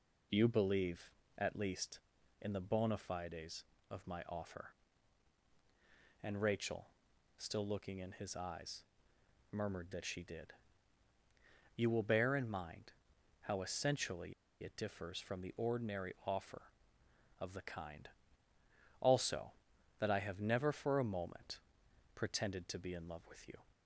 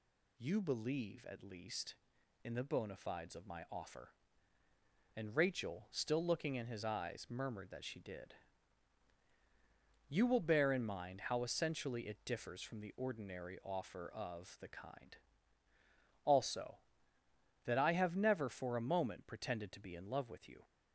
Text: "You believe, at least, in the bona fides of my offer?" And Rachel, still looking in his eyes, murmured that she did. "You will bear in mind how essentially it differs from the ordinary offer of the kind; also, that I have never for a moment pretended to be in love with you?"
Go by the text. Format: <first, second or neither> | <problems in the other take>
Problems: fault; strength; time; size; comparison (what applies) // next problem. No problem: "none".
second | pauses between "mind" and "how"; noticeable; at 12.9 s; 0.50 s long // pauses between "essentially" and "it"; slight; at 14.3 s; 0.29 s long // pauses between "moment" and "pretended"; noticeable; at 21.5 s; 0.56 s long